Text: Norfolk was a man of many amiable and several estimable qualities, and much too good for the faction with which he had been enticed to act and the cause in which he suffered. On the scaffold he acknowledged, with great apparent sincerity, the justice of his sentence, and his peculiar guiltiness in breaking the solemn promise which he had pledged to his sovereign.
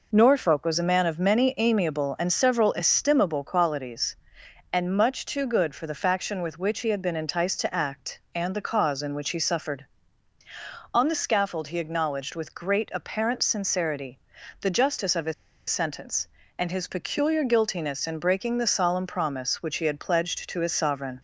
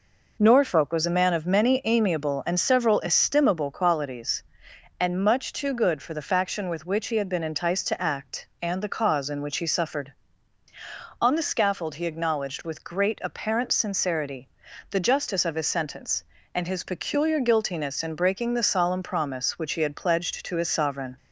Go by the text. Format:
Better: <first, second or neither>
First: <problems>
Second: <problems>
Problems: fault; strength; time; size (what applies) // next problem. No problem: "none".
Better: second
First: pauses between "his" and "sentence"; at 15.3 s; 0.36 s long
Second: none